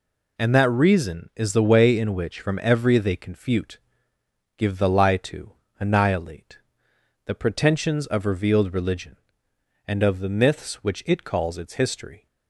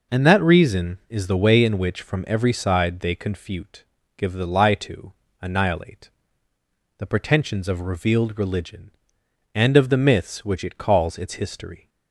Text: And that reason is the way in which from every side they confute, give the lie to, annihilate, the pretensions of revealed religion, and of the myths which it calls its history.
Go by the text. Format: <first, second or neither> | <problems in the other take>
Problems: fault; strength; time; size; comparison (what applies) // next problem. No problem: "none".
second | skips "side"; at 2.9 s